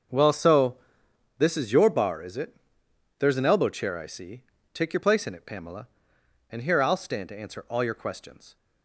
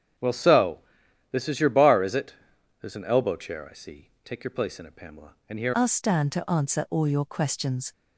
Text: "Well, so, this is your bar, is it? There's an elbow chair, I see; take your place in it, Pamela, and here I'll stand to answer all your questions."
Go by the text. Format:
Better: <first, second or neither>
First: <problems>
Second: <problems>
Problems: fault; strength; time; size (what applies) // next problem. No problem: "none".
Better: first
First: starts louder than the rest; until 1.7 s; 6.5 dB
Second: starts louder than the rest; strong; until 1.7 s; 8 dB // changes voice at "I'll"; from 5.7 s on; 2.2 s long